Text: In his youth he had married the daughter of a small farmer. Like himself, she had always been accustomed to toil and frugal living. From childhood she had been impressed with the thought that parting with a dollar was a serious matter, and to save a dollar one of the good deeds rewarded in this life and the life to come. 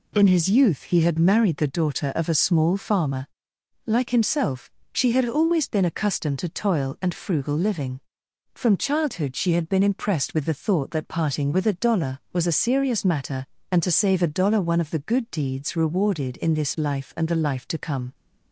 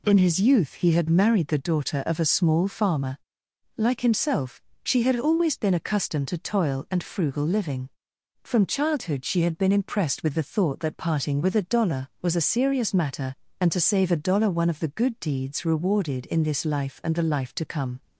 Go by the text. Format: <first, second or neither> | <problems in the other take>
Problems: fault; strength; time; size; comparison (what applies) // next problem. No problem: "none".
neither | none